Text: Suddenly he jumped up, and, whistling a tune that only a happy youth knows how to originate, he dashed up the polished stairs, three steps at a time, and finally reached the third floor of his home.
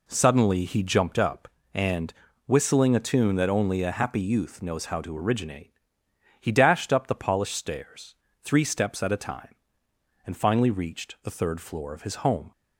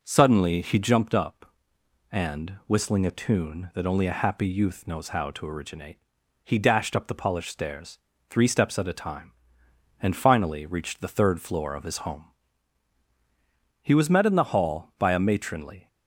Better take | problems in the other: first | goes on to say "He was met in the hall by a matronly"; strong; from 13.8 s on; 2.0 s long

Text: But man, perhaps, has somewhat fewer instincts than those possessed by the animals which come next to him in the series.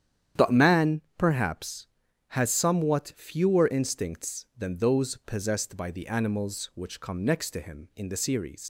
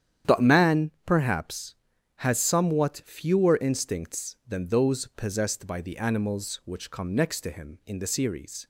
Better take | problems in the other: second | starts louder than the rest; strong; until 1.5 s; 9.5 dB; strong in the second // leaves "series" unfinished; at 8.6 s; 75 ms

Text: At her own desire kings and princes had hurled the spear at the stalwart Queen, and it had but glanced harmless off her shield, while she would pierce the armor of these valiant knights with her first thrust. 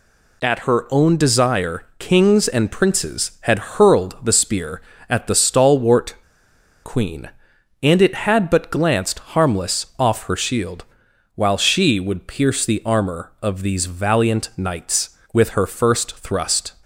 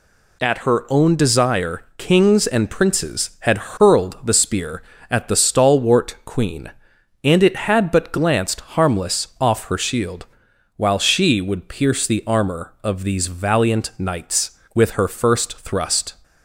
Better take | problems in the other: second | pauses between "stalwart" and "Queen"; noticeable; at 6.1 s; 0.70 s long

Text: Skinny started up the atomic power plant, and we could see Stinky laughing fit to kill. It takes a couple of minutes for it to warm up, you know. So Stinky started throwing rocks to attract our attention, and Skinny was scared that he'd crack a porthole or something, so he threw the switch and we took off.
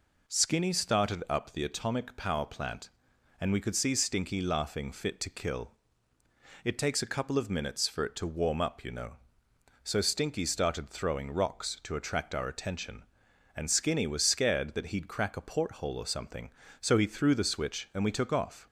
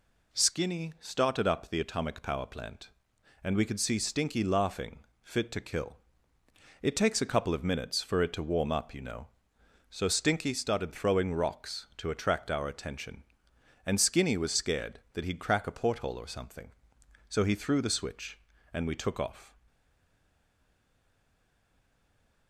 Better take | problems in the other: first | pauses between "laughing" and "fit"; slight; at 4.9 s; 0.24 s long // stays silent after the last word; strong; from 19.6 s on; 2.8 s long

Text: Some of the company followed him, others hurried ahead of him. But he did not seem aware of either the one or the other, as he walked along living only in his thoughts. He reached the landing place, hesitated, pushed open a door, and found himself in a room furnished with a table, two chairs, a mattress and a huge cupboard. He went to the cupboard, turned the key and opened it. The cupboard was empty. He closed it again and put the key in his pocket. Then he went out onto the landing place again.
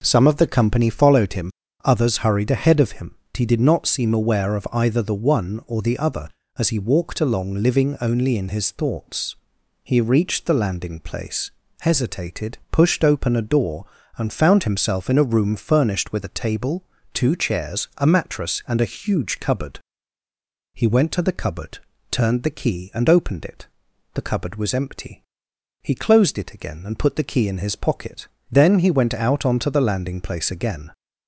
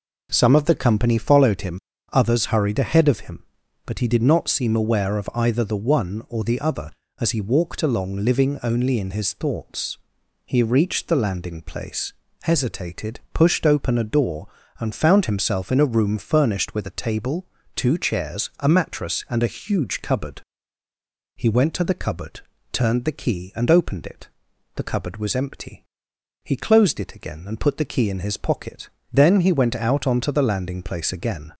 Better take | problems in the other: second | skips "But"; at 3.2 s

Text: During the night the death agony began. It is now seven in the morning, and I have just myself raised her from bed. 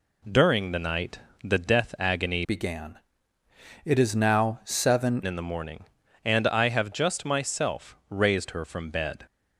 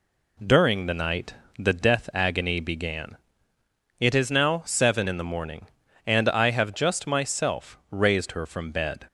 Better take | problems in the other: second | pauses between "night" and "the"; slight; at 1.1 s; 0.24 s long; slight in the second // changes voice from "began" to "seven"; from 2.4 to 5.2 s; 2.8 s long

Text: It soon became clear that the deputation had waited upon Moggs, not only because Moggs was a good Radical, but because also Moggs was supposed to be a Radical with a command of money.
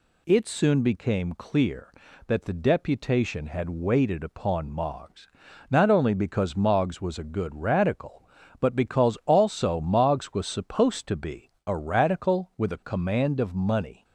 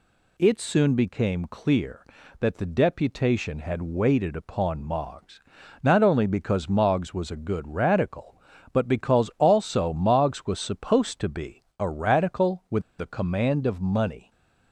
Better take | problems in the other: first | pauses between "be" and "a"; slight; at 11.6 s; 0.16 s long; slight in the first // pauses between "with" and "a"; slight; at 12.8 s; 0.17 s long

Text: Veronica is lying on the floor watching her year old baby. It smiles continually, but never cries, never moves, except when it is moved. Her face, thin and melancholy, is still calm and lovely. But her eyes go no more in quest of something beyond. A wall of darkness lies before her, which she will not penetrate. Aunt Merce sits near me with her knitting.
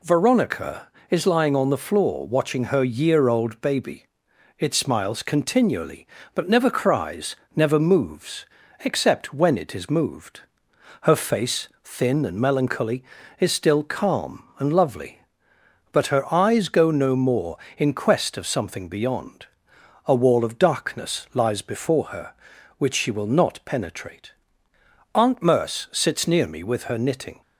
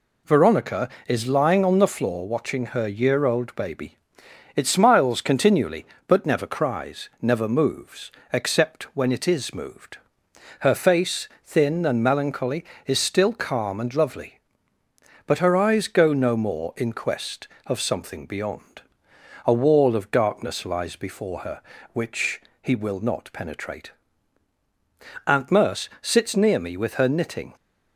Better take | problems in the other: first | says "he" for "she"; at 22.6 s

